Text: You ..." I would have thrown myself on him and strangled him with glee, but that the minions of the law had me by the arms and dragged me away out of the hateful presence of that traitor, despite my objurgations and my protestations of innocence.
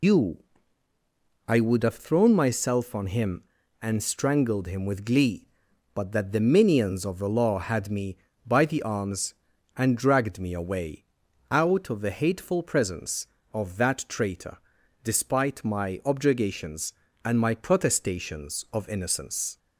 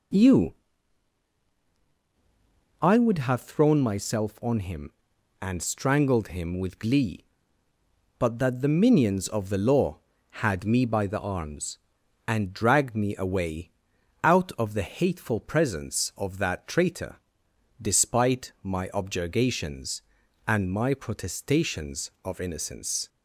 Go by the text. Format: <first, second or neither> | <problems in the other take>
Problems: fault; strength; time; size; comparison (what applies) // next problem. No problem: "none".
second | loses the start of "You"; at 0.0 s; 150 ms // pauses between "away" and "out"; at 11.0 s; 0.44 s long; noticeable in the second